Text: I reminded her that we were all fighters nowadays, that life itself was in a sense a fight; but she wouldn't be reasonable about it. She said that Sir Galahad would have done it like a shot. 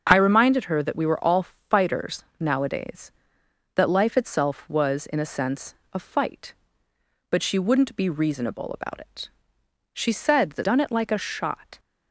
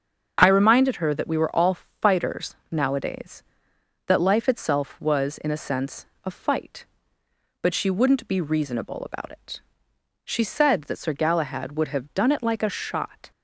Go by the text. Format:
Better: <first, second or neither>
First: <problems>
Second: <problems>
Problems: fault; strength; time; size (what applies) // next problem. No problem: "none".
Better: second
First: starts louder than the rest; until 1.1 s; 6.5 dB // pauses between "fighters" and "nowadays"; slight; at 2.2 s; 0.16 s long // pauses between "sense" and "a"; slight; at 5.7 s; 0.18 s long // skips "Sir Galahad would have"; at 10.6 s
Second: starts louder than the rest; until 1.4 s; 6.5 dB // pauses between "fighters" and "nowadays"; slight; at 2.5 s; 0.16 s long // pauses between "sense" and "a"; slight; at 6.0 s; 0.18 s long